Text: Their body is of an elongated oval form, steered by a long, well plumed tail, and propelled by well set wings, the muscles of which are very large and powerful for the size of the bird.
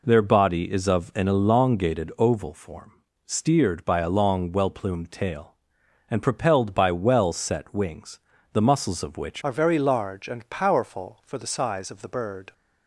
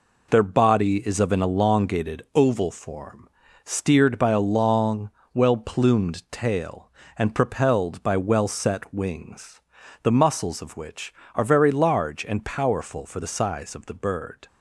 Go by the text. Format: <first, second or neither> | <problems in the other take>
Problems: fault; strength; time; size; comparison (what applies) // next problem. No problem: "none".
second | changes voice at "are"; from 9.4 s on; 3.1 s long